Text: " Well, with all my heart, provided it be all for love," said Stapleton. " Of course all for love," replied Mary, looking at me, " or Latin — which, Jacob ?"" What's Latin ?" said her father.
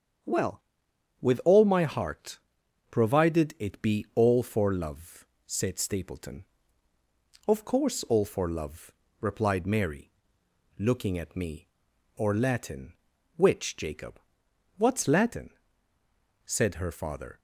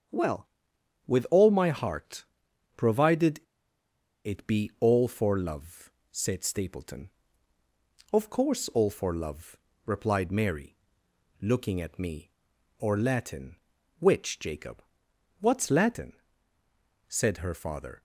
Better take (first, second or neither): first